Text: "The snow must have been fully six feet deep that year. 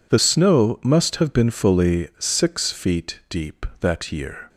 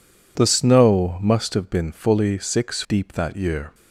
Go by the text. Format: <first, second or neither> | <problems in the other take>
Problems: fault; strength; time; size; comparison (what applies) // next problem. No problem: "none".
first | skips "feet"; at 2.8 s